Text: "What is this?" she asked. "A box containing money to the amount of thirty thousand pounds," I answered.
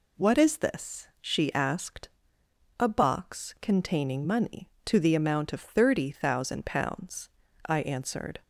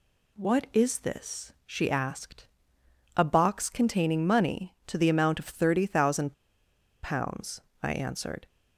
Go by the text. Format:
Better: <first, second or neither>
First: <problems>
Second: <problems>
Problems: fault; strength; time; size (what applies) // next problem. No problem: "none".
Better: first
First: none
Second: pauses between "thousand" and "pounds"; noticeable; at 6.3 s; 0.70 s long